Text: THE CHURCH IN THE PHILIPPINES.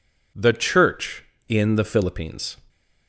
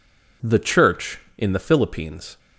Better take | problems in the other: neither | none

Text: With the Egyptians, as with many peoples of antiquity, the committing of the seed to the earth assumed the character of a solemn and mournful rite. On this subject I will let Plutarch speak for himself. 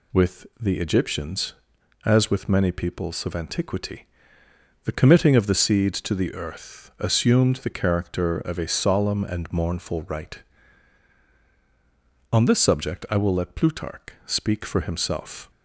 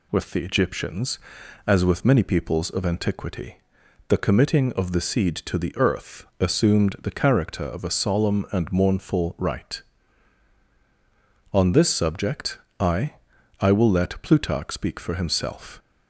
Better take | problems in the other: first | pauses between "earth" and "assumed"; slight; at 6.2 s; 0.16 s long // pauses between "subject" and "I"; slight; at 12.5 s; 0.20 s long // says "I" twice; at 13.6 s

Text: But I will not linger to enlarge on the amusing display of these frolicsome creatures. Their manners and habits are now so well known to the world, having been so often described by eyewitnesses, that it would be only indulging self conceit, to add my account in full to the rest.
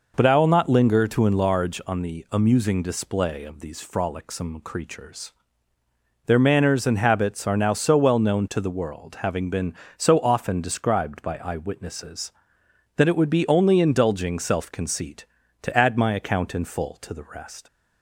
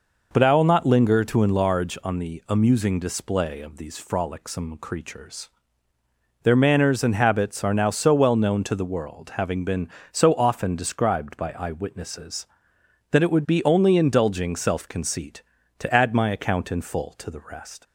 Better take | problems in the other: neither | none

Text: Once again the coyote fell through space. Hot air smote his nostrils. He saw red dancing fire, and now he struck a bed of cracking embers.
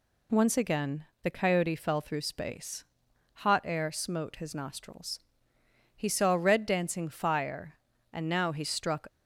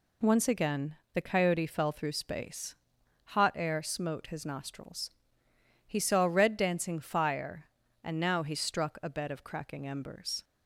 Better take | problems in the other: second | pauses between "again" and "the"; slight; at 1.0 s; 0.22 s long; slight in the second // stops before "a bed of cracking embers"; at 9.0 s

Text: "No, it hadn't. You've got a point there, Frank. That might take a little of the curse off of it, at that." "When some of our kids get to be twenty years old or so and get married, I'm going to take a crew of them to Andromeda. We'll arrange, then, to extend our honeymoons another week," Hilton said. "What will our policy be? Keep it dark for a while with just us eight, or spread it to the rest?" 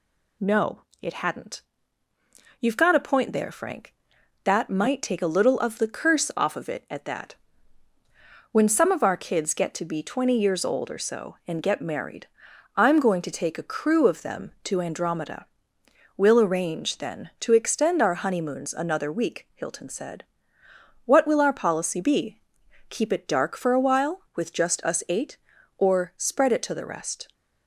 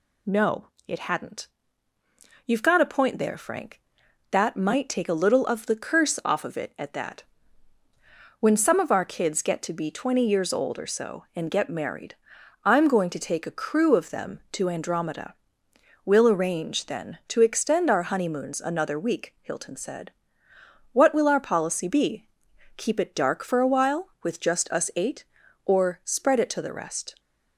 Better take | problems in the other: neither | none

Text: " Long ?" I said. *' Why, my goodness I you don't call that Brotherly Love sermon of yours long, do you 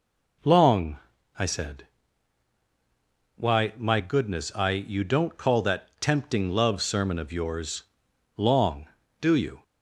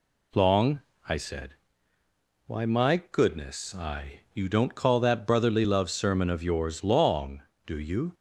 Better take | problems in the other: second | says "Tempting" for "Brotherly"; at 5.9 s // pauses between "yours" and "long"; noticeable; at 7.8 s; 0.52 s long

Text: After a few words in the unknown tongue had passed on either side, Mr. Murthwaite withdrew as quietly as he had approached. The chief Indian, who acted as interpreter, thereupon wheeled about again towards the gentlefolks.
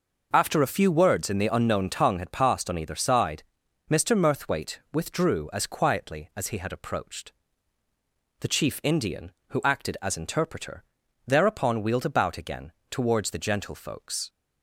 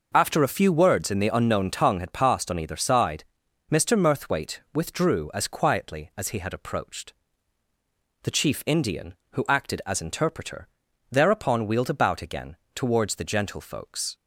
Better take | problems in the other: neither | pauses between "Murthwaite" and "withdrew"; slight; the same in both // pauses between "again" and "towards"; slight; the same in both

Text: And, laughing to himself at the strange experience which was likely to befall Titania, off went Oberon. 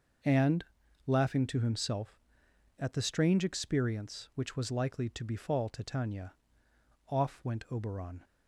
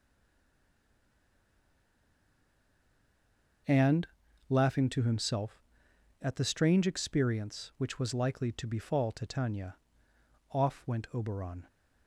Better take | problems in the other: first | stays silent before the first word; strong; until 3.6 s; 3.6 s long

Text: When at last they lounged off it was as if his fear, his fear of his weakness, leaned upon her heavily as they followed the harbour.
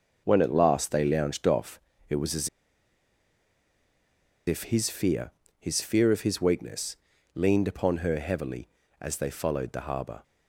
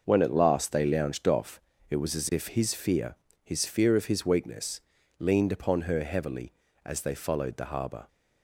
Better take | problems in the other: second | starts louder than the rest; noticeable; until 1.2 s; 6 dB; noticeable in the second // pauses between "off" and "it"; slight; at 1.7 s; 0.30 s long; slight in the second // pauses between "as" and "if"; strong; at 2.4 s; 1.9 s long

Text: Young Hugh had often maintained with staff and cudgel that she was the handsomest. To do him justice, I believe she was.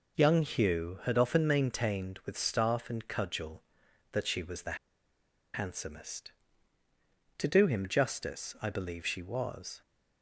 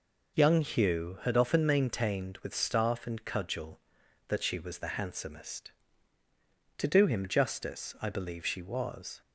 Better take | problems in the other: second | pauses between "the" and "handsomest"; noticeable; at 4.7 s; 0.77 s long

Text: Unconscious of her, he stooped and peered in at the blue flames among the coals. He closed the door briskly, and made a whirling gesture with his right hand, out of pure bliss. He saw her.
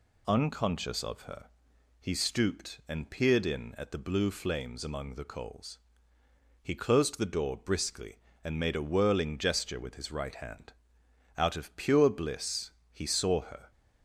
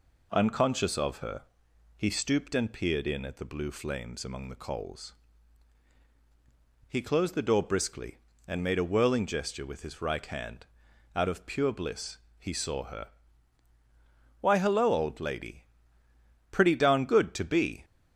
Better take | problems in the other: first | goes on to say "Why hello old lady Pretty darn good to be"; strong; from 14.4 s on; 3.4 s long

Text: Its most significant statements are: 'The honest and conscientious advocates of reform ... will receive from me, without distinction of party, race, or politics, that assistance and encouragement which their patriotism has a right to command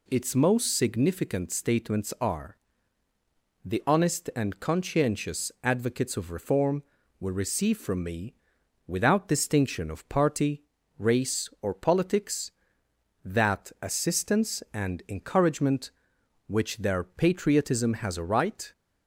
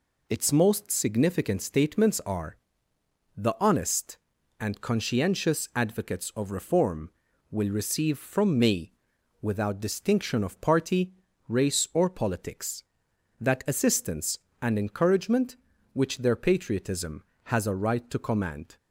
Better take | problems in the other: second | stops before "to command"; at 18.7 s

